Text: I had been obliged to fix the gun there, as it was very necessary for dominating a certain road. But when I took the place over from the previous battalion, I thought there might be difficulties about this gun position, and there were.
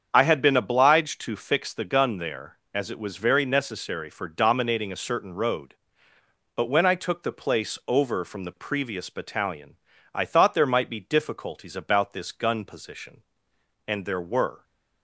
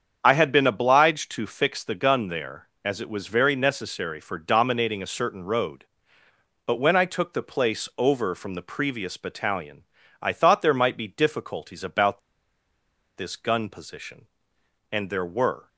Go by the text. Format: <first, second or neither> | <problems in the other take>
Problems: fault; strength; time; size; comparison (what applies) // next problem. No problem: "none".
first | starts louder than the rest; strong; until 1.2 s; 7.5 dB; strong in the first // pauses between "about" and "this"; at 12.2 s; 0.98 s long